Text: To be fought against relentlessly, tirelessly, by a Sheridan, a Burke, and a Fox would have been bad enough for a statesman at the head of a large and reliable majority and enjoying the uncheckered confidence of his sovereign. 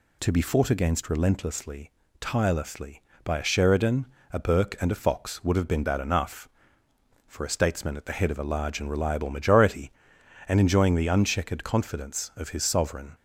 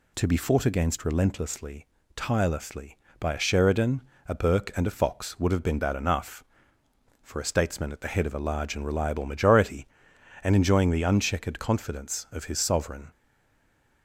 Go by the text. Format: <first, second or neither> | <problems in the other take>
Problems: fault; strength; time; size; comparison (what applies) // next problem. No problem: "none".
first | stays silent after the last word; slight; from 13.1 s on; 0.9 s long